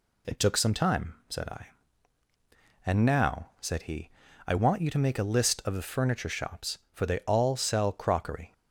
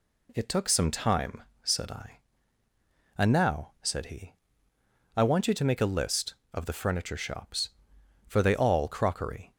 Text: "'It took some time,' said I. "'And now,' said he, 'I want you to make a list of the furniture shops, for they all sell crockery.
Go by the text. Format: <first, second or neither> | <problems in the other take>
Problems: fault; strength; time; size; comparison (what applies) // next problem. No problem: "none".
first | skips "sell"; at 8.8 s